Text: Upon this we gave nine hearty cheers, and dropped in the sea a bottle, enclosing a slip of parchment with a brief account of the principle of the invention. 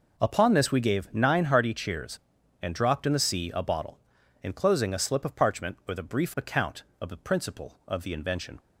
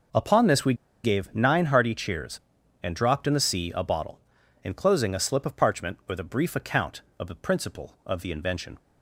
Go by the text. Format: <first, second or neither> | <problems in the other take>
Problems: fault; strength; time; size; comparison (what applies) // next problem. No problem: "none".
first | pauses between "we" and "gave"; slight; at 0.7 s; 0.29 s long